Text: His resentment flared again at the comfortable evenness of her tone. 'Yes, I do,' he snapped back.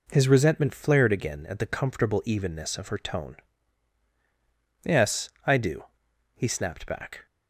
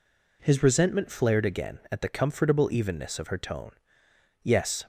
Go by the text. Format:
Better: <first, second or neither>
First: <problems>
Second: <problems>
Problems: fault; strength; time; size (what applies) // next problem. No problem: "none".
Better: first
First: none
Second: stops before "I do he snapped back"; at 4.8 s